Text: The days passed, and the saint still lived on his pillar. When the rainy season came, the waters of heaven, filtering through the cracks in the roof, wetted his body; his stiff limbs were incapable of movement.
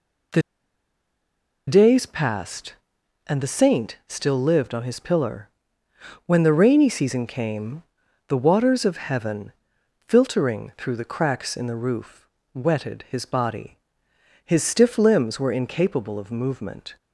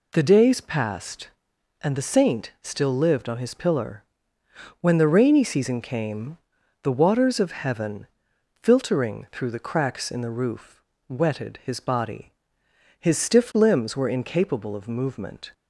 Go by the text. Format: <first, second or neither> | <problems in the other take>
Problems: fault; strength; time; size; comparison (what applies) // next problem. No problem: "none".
second | pauses between "The" and "days"; strong; at 0.4 s; 1.2 s long